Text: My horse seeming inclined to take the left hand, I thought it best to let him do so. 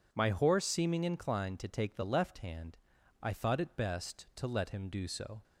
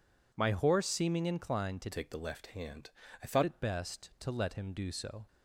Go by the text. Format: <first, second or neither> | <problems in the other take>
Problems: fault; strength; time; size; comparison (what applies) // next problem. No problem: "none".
first | changes voice from "take" to "thought"; from 1.9 to 3.4 s; 1.5 s long